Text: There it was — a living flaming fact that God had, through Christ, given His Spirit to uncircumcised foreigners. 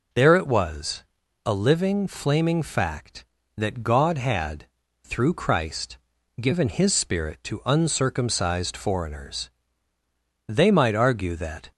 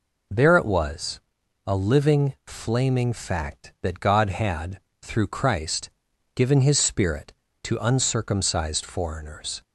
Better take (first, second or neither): second